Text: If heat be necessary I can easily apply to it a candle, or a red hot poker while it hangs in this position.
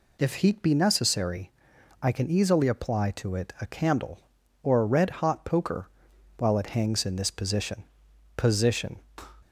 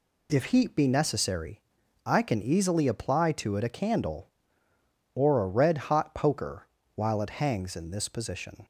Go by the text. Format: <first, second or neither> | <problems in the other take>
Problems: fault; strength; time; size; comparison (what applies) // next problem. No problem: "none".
second | pauses between "necessary" and "I"; noticeable; at 1.4 s; 0.50 s long; also in the second // pauses between "poker" and "while"; noticeable; at 5.8 s; 0.50 s long; slight in the second // says "position" twice; at 8.3 s